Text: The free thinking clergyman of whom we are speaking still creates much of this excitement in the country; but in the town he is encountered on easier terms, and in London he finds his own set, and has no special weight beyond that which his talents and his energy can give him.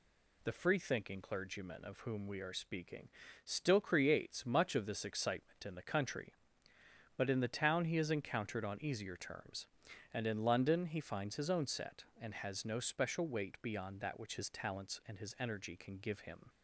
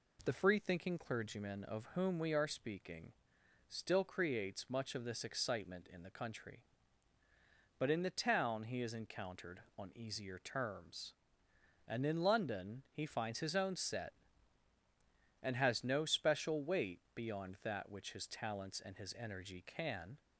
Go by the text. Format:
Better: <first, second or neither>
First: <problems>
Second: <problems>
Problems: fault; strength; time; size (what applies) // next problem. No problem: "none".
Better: first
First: pauses between "speaking" and "still"; slight; at 3.0 s; 0.36 s long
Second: pauses between "speaking" and "still"; noticeable; at 3.1 s; 0.56 s long // stops before "give him"; at 20.1 s